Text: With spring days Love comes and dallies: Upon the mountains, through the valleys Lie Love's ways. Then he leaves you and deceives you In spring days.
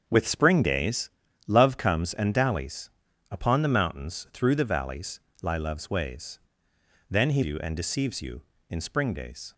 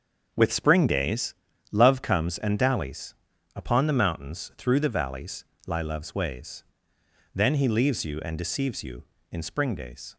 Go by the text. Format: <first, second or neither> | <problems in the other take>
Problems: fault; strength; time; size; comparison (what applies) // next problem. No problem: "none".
second | starts louder than the rest; until 1.0 s; 7 dB; also in the second // pauses between "days" and "Love"; at 1.1 s; 0.38 s long; also in the second // pauses between "valleys" and "Lie"; slight; at 5.1 s; 0.24 s long; slight in the second // skips "leaves"; at 7.4 s